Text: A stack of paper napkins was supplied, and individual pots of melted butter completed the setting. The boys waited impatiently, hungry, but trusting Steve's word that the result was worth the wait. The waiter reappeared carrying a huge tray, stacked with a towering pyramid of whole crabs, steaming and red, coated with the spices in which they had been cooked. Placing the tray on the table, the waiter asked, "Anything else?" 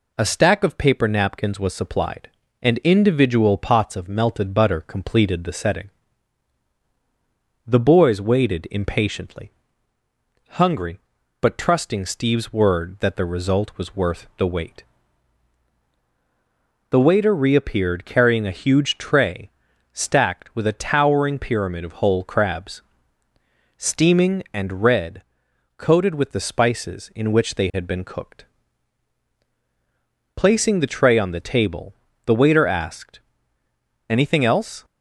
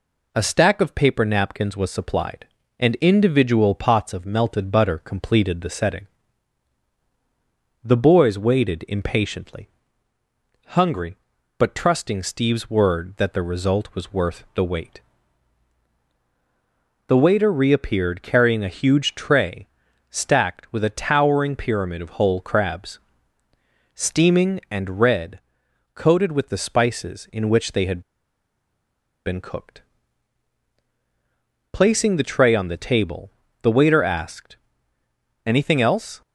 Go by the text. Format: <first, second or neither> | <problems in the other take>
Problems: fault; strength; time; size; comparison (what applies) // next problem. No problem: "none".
first | pauses between "had" and "been"; strong; at 28.0 s; 1.2 s long